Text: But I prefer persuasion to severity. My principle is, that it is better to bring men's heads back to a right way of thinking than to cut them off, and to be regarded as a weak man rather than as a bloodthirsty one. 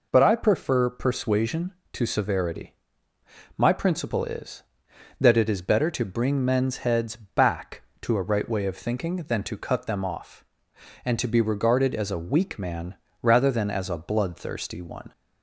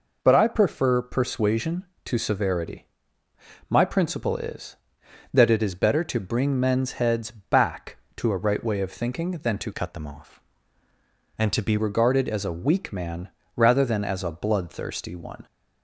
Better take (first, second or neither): first